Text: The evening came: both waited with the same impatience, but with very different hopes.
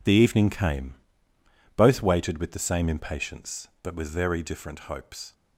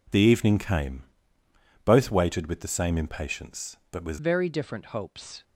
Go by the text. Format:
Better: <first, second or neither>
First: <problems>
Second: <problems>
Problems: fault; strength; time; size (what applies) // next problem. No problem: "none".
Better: first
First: none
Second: changes voice at "very"; from 4.1 s on; 1.3 s long